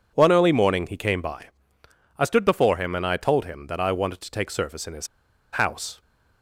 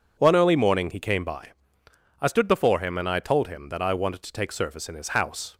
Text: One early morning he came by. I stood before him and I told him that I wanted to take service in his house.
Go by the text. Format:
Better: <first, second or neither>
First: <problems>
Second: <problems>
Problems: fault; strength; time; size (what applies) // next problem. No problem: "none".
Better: second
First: pauses between "his" and "house"; at 5.0 s; 0.45 s long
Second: none